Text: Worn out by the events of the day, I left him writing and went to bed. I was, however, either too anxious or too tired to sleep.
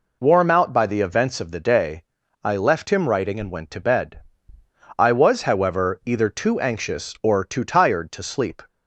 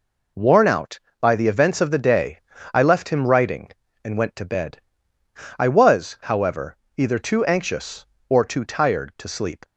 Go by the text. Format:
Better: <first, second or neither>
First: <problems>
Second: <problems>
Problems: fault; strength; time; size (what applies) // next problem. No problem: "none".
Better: second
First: says "Warm" for "Worn"; at 0.2 s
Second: none